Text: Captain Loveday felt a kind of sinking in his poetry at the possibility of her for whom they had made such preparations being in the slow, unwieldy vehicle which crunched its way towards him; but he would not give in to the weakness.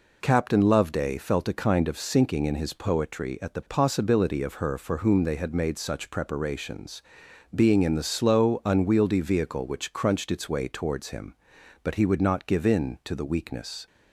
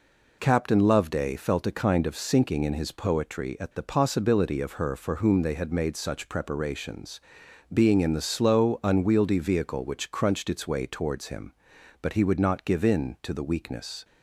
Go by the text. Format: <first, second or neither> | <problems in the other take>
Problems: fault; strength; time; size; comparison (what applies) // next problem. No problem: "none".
neither | pauses between "preparations" and "being"; noticeable; the same in both